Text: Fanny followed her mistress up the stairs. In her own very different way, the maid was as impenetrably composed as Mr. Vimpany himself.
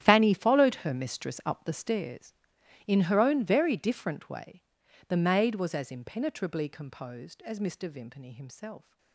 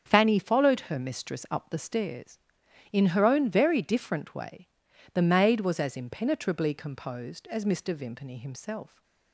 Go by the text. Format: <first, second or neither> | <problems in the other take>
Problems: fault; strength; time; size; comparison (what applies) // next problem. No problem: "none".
second | gets quieter; strong; throughout; 16.5 dB // starts louder than the rest; strong; until 1.0 s; 11.5 dB; strong in the second